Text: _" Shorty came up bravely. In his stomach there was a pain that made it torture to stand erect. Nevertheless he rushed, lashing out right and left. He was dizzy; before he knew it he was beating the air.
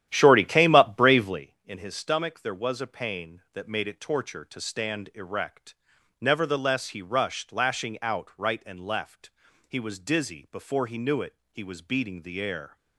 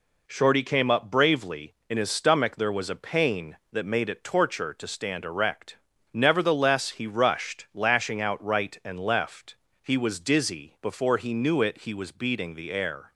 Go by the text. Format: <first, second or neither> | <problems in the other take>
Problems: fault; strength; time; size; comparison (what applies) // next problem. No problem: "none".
second | starts louder than the rest; strong; until 1.5 s; 11.5 dB // pauses between "it" and "he"; slight; at 11.3 s; 0.16 s long